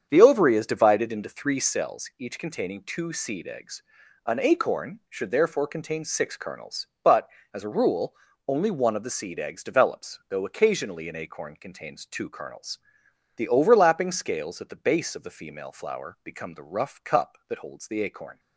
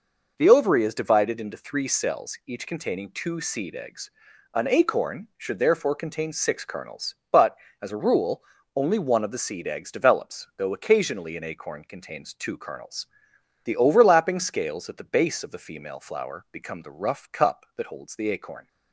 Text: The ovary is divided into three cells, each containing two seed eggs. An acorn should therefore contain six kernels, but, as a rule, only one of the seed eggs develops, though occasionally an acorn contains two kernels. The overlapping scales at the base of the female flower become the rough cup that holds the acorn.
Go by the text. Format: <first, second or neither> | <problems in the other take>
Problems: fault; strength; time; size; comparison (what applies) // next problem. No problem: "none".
second | starts louder than the rest; strong; until 1.8 s; 7.5 dB